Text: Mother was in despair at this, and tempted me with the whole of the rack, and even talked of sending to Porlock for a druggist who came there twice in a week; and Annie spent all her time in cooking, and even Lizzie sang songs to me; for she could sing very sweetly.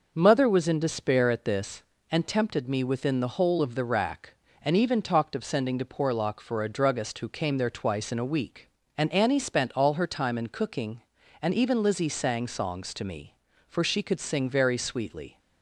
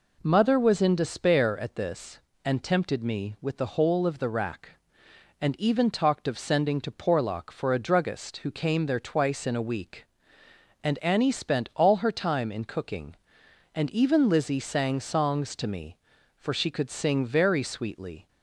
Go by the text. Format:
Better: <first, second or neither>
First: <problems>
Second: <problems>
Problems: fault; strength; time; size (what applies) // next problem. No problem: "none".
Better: second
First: says "within" for "with"; at 2.8 s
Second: none